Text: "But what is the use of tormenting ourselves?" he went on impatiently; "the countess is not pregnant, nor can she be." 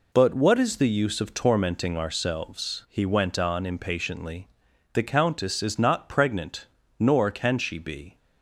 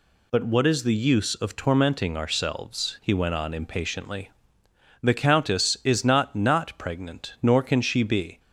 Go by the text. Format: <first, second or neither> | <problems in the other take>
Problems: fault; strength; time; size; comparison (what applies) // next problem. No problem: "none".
first | says "not" twice; at 6.3 s